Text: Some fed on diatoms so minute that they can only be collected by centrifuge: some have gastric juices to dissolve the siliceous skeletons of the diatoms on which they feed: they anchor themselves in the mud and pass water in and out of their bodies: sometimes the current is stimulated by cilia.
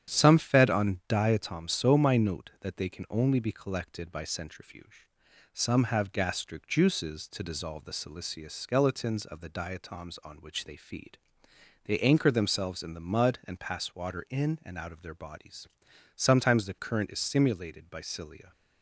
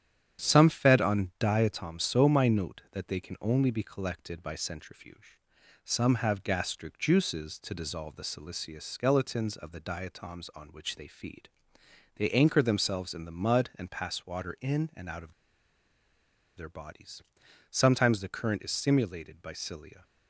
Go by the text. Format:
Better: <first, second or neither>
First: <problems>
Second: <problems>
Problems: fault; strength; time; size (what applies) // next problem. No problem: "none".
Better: first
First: starts louder than the rest; strong; until 1.1 s; 9.5 dB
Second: starts louder than the rest; strong; until 1.4 s; 9.5 dB // pauses between "of" and "their"; at 15.3 s; 1.2 s long